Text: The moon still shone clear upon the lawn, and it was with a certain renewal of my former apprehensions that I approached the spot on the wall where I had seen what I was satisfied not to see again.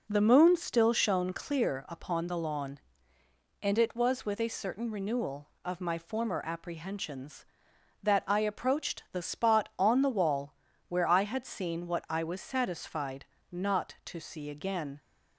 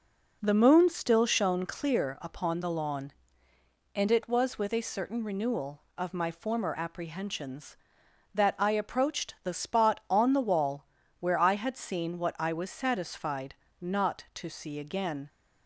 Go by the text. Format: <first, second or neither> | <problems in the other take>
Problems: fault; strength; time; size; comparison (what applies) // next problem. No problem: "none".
neither | pauses between "wall" and "where"; slight; the same in both // pauses between "satisfied" and "not"; slight; the same in both